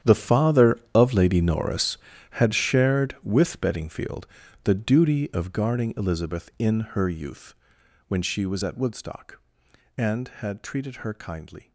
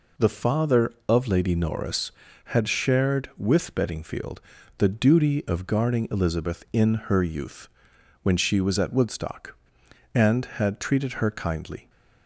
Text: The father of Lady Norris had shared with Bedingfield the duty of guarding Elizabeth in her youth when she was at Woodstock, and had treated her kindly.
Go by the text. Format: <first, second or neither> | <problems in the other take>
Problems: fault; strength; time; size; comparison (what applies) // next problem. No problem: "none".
second | gets quieter; strong; throughout; 16.5 dB // pauses between "Bedingfield" and "the"; at 4.2 s; 0.38 s long; also in the second // pauses between "youth" and "when"; noticeable; at 7.5 s; 0.53 s long; noticeable in the second